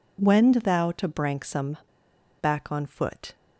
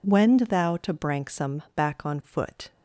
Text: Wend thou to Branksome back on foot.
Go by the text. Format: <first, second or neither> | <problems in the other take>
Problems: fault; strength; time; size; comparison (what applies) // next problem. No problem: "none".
second | pauses between "Branksome" and "back"; noticeable; at 1.7 s; 0.63 s long